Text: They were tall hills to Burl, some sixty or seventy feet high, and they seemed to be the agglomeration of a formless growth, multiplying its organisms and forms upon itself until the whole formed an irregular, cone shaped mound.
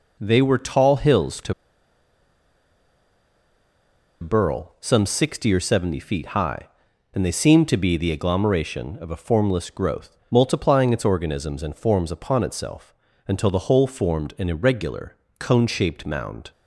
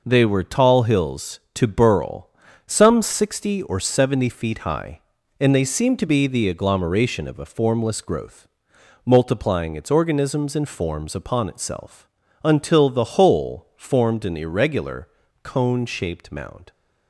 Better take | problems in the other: second | pauses between "to" and "Burl"; strong; at 1.5 s; 2.6 s long // pauses between "itself" and "until"; slight; at 12.9 s; 0.34 s long; also in the second

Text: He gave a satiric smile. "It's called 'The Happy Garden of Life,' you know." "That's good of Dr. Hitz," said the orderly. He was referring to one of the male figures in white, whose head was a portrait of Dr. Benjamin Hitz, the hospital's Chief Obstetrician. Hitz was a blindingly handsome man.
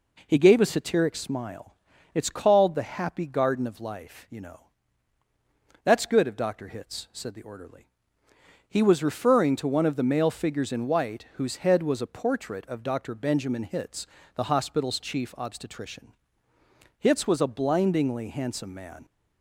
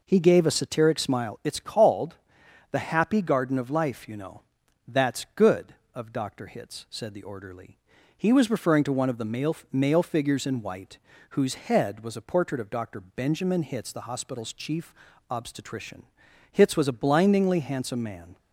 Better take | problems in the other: first | pauses between "called" and "The"; noticeable; at 2.1 s; 0.56 s long // says "male" twice; at 9.7 s // pauses between "Chief" and "Obstetrician"; at 14.9 s; 0.38 s long

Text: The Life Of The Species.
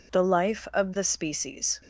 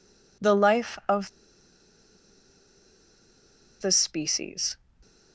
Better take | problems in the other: first | pauses between "Of" and "The"; strong; at 1.2 s; 2.5 s long

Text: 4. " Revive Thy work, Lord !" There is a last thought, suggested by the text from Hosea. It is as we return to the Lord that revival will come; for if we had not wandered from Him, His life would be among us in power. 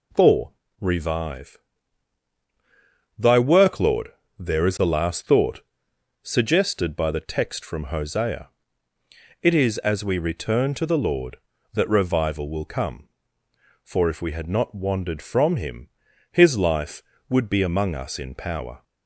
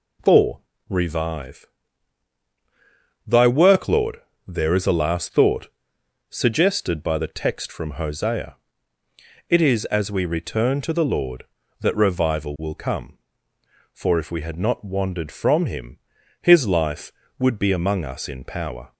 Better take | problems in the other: neither | pauses between "Revive" and "Thy"; strong; the same in both

